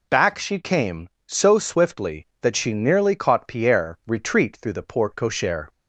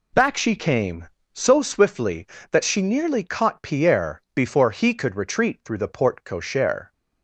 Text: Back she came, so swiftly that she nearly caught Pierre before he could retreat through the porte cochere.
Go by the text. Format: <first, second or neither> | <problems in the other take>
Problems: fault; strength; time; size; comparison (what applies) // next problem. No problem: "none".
second | skips "before he could"; at 4.0 s